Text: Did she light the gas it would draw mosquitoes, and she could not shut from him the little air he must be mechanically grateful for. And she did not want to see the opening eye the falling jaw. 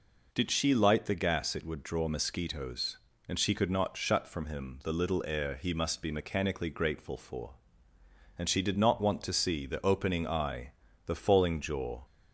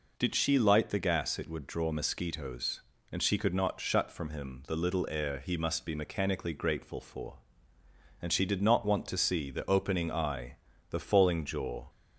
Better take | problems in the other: neither | pauses between "eye" and "the"; slight; the same in both

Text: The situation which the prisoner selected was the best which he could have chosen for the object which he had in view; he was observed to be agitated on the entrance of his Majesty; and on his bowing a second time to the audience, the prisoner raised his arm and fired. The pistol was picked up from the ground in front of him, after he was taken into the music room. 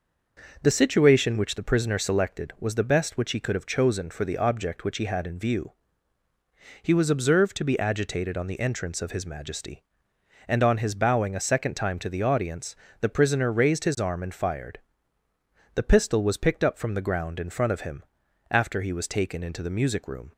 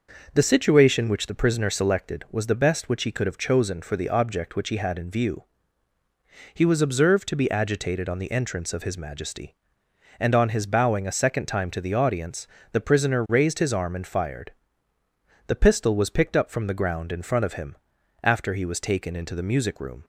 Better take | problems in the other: neither | none

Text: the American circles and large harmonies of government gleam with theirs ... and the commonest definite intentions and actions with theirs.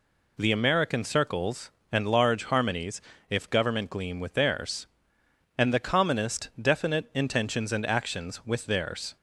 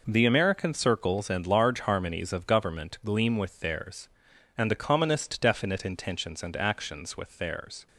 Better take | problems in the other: second | says "if" for "of"; at 3.3 s

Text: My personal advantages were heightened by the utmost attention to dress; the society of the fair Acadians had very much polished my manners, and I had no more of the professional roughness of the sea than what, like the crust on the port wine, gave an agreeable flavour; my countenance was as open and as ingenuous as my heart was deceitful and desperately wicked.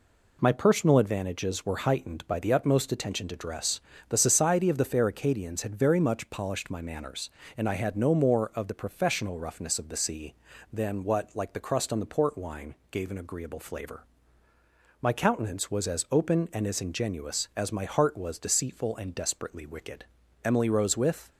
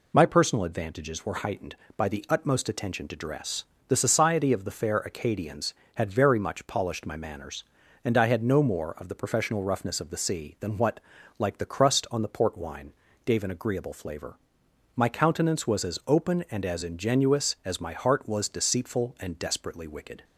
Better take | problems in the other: second | goes on to say "Emily rose with"; noticeable; from 20.4 s on; 0.88 s long

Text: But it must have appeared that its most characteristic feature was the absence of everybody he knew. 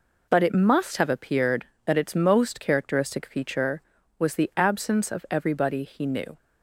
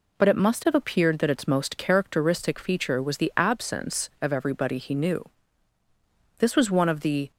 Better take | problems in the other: first | goes on to say "This was one of the"; noticeable; from 6.3 s on; 0.92 s long

